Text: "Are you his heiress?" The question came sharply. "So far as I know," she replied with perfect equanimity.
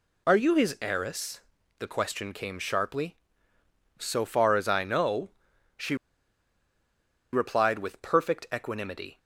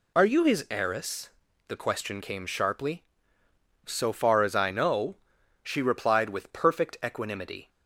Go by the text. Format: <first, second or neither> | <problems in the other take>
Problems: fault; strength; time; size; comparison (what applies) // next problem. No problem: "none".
second | pauses between "she" and "replied"; strong; at 5.9 s; 1.3 s long